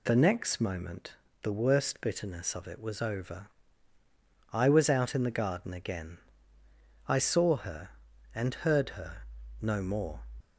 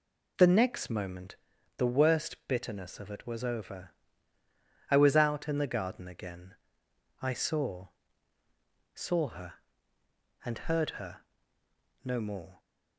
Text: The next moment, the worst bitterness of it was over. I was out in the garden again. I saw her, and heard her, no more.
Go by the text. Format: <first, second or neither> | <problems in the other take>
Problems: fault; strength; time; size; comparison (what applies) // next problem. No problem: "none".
first | says "saw" twice; at 8.9 s